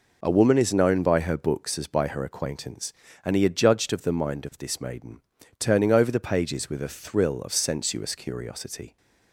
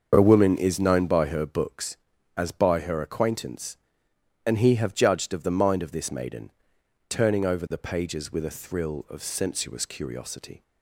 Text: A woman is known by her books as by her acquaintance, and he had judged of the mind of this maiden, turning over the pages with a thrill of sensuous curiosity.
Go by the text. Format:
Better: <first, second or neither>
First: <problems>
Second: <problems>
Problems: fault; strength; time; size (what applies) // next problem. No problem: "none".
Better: first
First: none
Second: starts louder than the rest; until 1.1 s; 6.5 dB // says "have" for "had"; at 4.7 s